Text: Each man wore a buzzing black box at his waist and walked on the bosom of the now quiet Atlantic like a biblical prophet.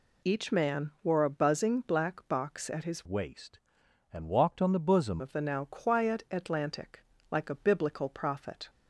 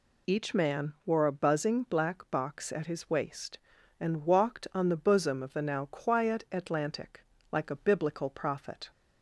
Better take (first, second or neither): second